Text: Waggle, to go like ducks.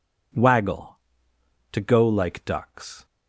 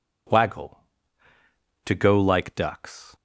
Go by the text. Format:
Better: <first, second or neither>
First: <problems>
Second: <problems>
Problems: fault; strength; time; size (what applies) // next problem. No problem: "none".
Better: neither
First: none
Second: none